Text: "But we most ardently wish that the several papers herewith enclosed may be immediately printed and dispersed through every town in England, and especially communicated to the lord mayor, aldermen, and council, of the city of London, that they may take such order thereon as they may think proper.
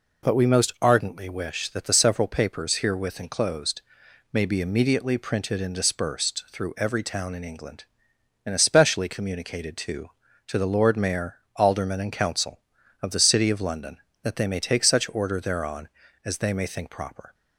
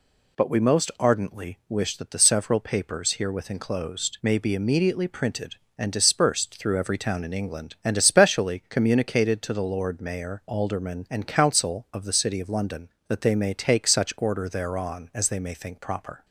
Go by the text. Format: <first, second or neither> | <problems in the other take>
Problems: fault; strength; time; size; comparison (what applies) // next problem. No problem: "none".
second | pauses between "enclosed" and "may"; noticeable; at 3.8 s; 0.50 s long // says "to" twice; at 10.4 s